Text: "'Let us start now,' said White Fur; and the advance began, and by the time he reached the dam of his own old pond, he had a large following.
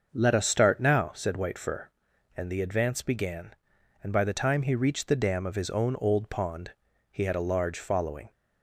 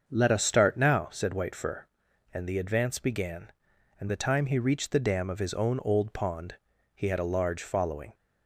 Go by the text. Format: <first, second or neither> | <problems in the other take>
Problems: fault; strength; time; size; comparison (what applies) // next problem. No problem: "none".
first | starts louder than the rest; until 1.0 s; 6.5 dB; also in the first // skips "by"; at 4.0 s